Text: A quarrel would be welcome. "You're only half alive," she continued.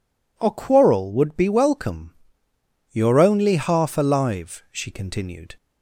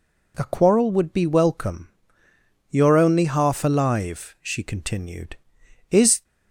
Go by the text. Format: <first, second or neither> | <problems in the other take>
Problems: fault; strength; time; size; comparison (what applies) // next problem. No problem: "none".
first | goes on to say "Is"; slight; from 5.8 s on; 0.34 s long